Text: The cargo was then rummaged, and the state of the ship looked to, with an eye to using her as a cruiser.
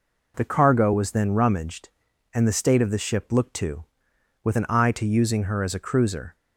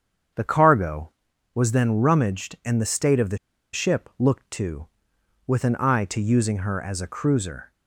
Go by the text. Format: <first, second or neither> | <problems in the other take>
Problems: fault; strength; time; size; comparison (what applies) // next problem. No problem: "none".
first | starts louder than the rest; strong; until 1.7 s; 7.5 dB // pauses between "the" and "ship"; at 3.3 s; 0.36 s long